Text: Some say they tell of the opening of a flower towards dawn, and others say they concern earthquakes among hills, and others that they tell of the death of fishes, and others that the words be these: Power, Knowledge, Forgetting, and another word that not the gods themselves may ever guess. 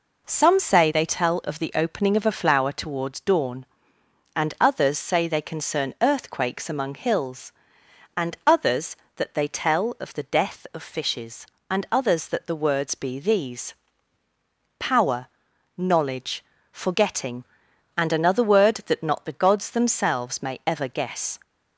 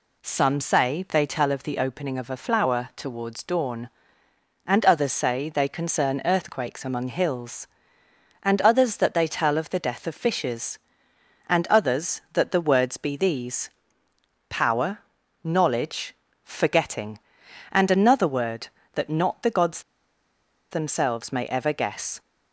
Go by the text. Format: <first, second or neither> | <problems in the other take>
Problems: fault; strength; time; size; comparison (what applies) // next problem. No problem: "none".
first | pauses between "gods" and "themselves"; noticeable; at 19.7 s; 0.91 s long